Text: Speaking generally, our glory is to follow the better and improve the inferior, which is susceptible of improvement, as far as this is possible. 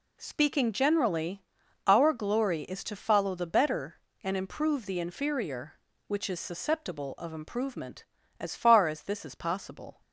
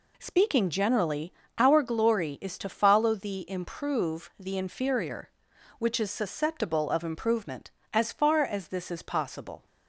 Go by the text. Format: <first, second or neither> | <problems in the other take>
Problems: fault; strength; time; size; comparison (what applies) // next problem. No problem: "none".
first | skips "better and"; at 3.4 s